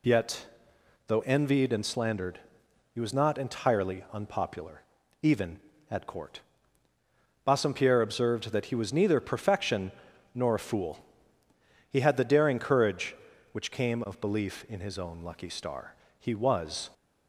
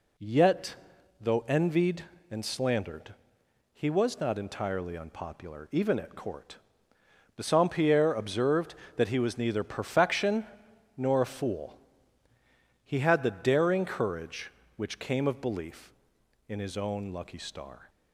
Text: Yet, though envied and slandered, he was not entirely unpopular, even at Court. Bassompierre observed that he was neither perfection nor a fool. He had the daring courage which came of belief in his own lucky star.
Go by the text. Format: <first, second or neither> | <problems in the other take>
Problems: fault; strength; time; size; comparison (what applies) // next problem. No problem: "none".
second | pauses between "perfection" and "nor"; at 9.9 s; 0.44 s long; noticeable in the second // goes on to say "He was"; noticeable; from 16.1 s on; 0.70 s long